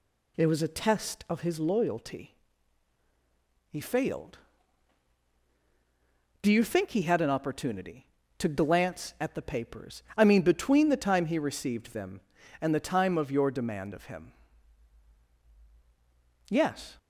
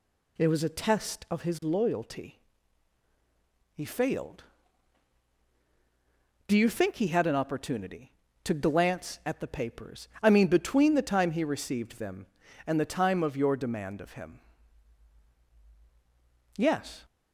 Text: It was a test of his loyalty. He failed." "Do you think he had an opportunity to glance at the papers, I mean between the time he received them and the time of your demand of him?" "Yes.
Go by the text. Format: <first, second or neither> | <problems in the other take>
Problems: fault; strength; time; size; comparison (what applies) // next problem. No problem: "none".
neither | none